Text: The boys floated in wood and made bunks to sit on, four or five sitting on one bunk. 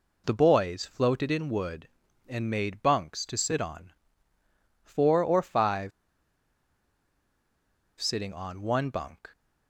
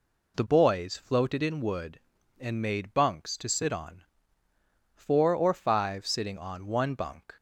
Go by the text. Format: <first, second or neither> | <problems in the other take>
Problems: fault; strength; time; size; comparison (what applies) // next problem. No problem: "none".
second | pauses between "five" and "sitting"; strong; at 5.9 s; 2.0 s long